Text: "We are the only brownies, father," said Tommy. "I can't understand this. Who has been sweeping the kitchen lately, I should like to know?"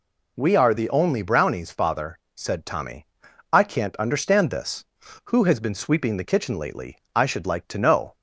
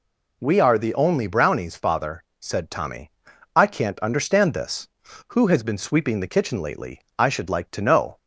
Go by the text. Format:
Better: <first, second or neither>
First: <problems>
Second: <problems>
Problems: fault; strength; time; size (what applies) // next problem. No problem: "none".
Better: neither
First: none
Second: none